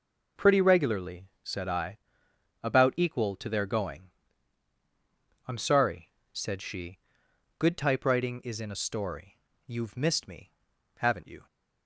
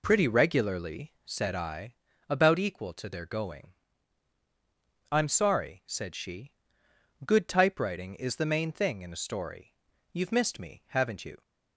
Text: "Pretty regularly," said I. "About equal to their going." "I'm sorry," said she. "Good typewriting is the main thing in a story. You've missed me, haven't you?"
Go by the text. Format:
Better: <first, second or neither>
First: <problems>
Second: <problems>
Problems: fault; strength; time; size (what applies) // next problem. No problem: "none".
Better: second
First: skips "the main thing"; at 8.5 s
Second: none